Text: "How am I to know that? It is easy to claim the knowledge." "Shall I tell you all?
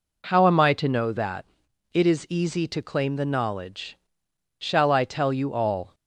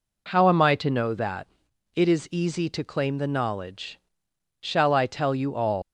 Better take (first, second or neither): first